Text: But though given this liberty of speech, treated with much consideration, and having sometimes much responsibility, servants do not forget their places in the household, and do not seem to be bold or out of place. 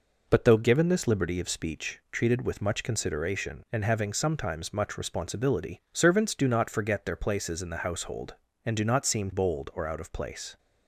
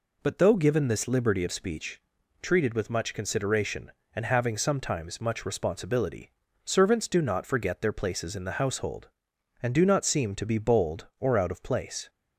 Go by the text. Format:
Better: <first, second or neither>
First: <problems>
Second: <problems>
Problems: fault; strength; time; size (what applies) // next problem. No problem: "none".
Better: second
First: skips "to be"; at 9.3 s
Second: none